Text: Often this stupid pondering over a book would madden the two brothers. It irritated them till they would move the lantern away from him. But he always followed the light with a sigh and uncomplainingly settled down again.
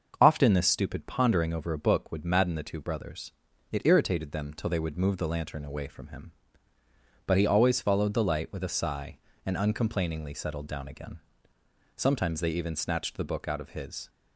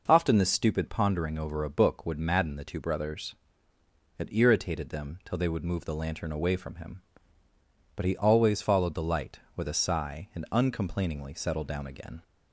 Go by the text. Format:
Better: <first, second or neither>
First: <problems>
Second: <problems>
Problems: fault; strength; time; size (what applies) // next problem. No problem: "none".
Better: second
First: starts louder than the rest; until 1.2 s; 6 dB // goes on to say "Sometimes they even snatched the book out of his"; strong; from 11.9 s on; 2.1 s long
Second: none